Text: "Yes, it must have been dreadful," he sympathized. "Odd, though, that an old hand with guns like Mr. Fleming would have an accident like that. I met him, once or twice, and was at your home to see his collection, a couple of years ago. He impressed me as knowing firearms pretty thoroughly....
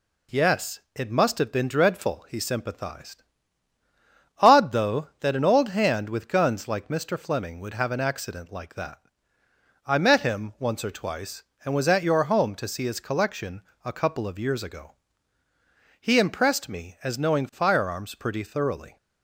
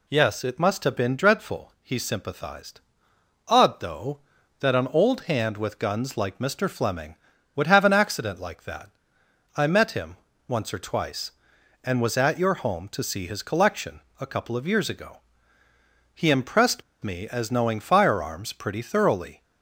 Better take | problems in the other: first | pauses between "impressed" and "me"; slight; at 16.8 s; 0.21 s long

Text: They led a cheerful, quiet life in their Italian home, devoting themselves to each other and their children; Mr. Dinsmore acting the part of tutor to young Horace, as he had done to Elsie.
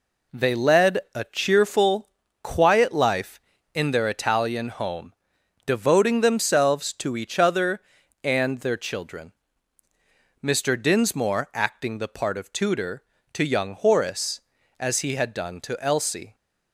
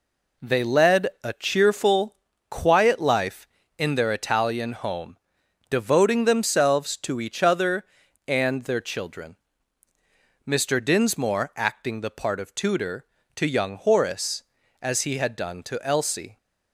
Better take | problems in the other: neither | pauses between "led" and "a"; slight; the same in both

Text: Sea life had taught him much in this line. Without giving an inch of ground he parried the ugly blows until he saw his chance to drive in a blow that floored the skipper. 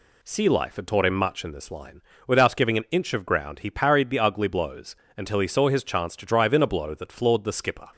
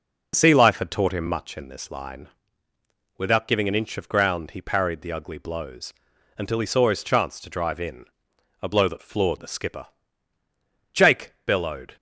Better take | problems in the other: first | pauses between "blows" and "until"; at 5.9 s; 0.42 s long; slight in the first // pauses between "in" and "a"; noticeable; at 8.0 s; 0.54 s long // goes on to say "Jake bellowed"; noticeable; from 10.9 s on; 1.0 s long

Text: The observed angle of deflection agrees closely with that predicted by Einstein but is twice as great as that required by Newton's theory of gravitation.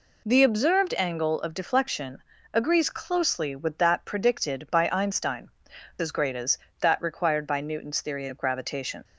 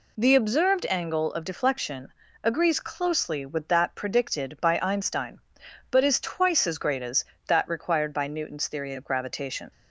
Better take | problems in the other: second | pauses between "deflection" and "agrees"; slight; at 2.2 s; 0.30 s long; slight in the second // skips "but is twice"; at 5.7 s

